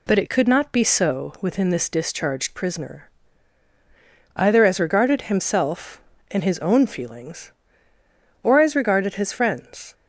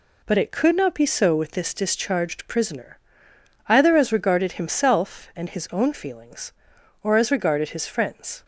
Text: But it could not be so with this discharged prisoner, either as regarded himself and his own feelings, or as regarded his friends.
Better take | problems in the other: second | says "within" for "with"; at 1.4 s

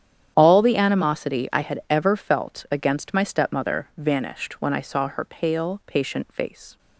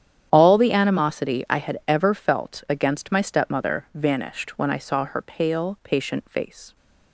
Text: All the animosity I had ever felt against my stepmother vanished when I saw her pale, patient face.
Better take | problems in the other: neither | starts louder than the rest; strong; the same in both

